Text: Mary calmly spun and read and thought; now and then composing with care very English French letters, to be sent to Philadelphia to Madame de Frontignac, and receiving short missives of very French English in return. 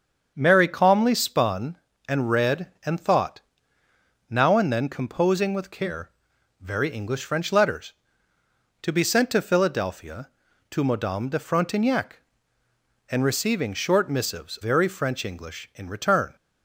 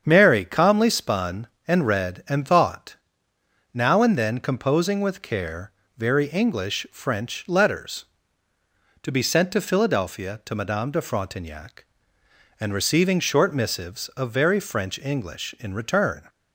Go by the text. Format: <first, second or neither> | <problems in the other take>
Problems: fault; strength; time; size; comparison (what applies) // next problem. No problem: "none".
second | starts louder than the rest; until 1.3 s; 7 dB; strong in the second // pauses between "care" and "very"; noticeable; at 6.0 s; 0.52 s long; slight in the second // skips "of"; at 14.5 s